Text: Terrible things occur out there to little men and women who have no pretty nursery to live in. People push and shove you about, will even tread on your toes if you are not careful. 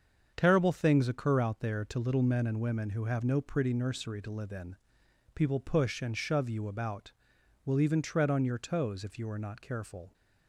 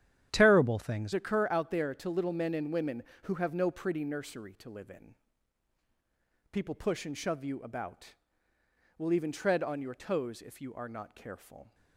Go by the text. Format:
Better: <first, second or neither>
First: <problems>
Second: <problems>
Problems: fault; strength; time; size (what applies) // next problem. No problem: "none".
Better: first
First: starts louder than the rest; strong; until 1.3 s; 7 dB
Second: starts louder than the rest; strong; until 1.3 s; 10 dB // changes voice at "occur"; from 1.1 s on; 10.6 s long